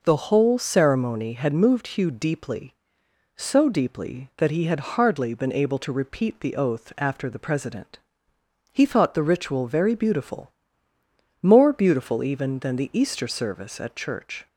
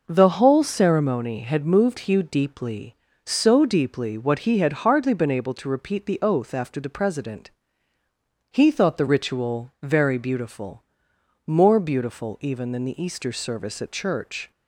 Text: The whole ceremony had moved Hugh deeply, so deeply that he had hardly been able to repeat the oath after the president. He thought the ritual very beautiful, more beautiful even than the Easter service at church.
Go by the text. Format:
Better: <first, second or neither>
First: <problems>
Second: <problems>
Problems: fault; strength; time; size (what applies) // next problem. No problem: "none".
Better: first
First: none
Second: says "what" for "that"; at 4.1 s